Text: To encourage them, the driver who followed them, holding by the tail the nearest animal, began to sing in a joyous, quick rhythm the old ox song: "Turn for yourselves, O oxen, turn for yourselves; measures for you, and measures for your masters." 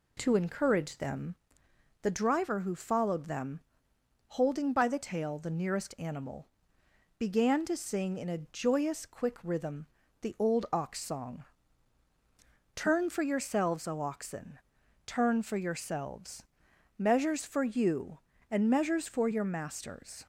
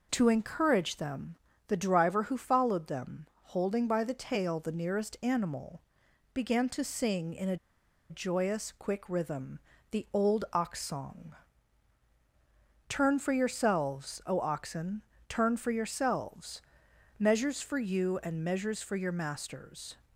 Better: first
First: pauses between "rhythm" and "the"; slight; at 9.8 s; 0.36 s long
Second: pauses between "a" and "joyous"; noticeable; at 7.5 s; 0.53 s long // pauses between "rhythm" and "the"; slight; at 9.5 s; 0.32 s long

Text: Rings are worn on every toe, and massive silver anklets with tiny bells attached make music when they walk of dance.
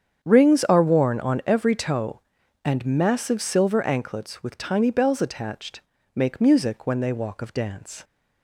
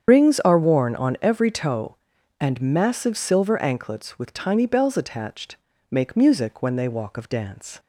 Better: first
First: starts louder than the rest; strong; until 1.2 s; 8 dB // pauses between "attached" and "make"; slight; at 5.7 s; 0.34 s long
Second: loses the start of "Rings"; at 0.0 s; 90 ms // starts louder than the rest; strong; until 1.1 s; 8 dB // pauses between "attached" and "make"; slight; at 5.5 s; 0.34 s long

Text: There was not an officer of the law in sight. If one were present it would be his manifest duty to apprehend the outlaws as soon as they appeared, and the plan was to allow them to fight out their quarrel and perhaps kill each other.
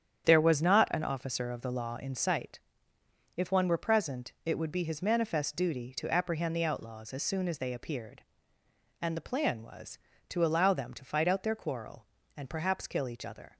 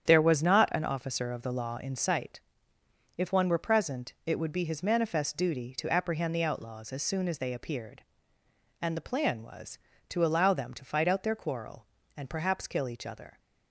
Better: neither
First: starts louder than the rest; strong; until 1.2 s; 9 dB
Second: starts louder than the rest; strong; until 1.0 s; 9 dB

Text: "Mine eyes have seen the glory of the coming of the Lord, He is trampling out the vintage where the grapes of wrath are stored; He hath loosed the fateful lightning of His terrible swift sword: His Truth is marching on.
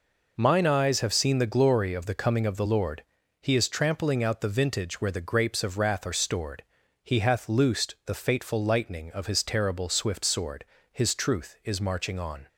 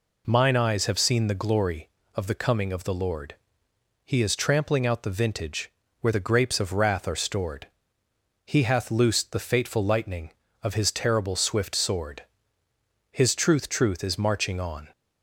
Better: first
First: none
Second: pauses between "vintage" and "where"; slight; at 5.6 s; 0.30 s long // says "Truth" twice; at 13.6 s

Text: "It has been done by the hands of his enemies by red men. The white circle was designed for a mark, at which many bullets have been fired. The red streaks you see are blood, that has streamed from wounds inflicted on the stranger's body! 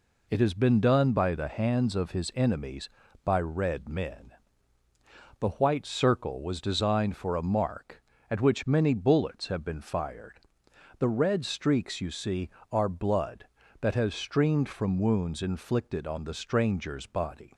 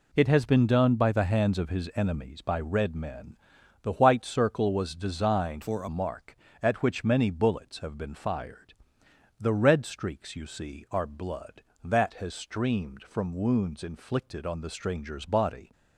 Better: first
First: none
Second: changes voice from "for" to "a"; from 5.6 to 5.8 s; 0.2 s long

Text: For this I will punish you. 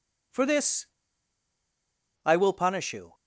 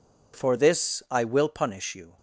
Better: second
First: pauses between "this" and "I"; strong; at 0.8 s; 1.3 s long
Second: none

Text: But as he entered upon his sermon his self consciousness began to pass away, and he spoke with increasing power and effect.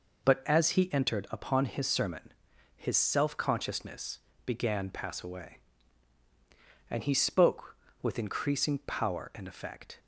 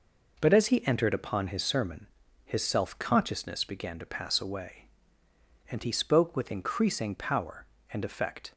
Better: second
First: pauses between "sermon" and "his"; at 2.3 s; 0.42 s long // pauses between "consciousness" and "began"; slight; at 4.1 s; 0.28 s long // skips "to"; at 4.8 s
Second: pauses between "sermon" and "his"; at 2.0 s; 0.38 s long

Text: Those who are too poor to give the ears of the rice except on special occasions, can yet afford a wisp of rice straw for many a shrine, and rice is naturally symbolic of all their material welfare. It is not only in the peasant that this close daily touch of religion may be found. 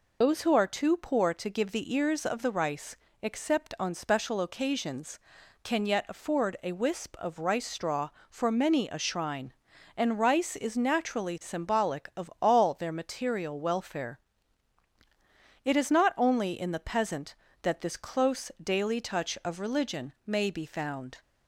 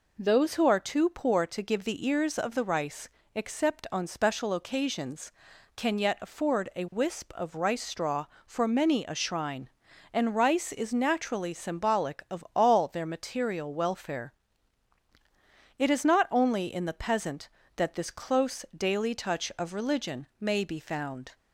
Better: second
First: loses the start of "Those"; at 0.2 s; 155 ms // pauses between "rice" and "except"; slight; at 2.9 s; 0.28 s long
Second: pauses between "rice" and "except"; slight; at 3.0 s; 0.28 s long

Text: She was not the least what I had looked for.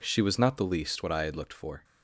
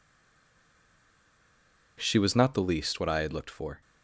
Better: first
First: none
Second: stays silent before the first word; noticeable; until 1.9 s; 1.9 s long

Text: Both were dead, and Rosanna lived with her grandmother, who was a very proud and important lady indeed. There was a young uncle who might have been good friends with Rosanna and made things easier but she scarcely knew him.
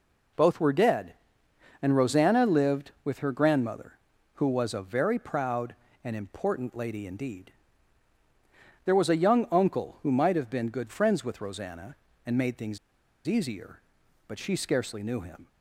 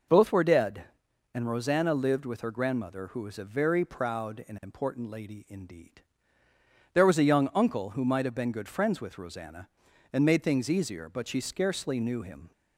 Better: second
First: pauses between "things" and "easier"; noticeable; at 12.7 s; 0.49 s long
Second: none

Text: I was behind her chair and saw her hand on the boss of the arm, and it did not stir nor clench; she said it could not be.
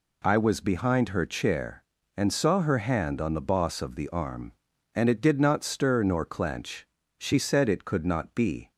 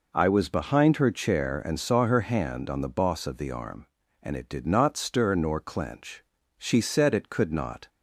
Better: first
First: none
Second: stops before "be"; at 7.8 s

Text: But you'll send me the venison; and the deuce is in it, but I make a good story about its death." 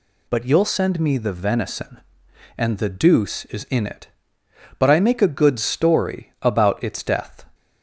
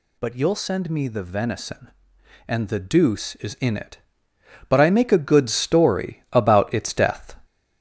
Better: first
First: none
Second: gets louder; noticeable; throughout; 4.5 dB

